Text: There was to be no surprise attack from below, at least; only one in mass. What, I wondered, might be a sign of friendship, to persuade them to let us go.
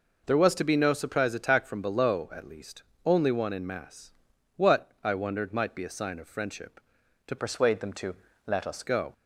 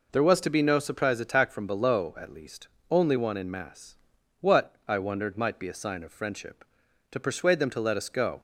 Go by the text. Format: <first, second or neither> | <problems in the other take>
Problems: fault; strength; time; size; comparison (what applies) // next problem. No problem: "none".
second | changes voice from "persuade" to "us"; from 7.3 to 8.8 s; 1.5 s long // pauses between "to" and "let"; slight; at 8.1 s; 0.30 s long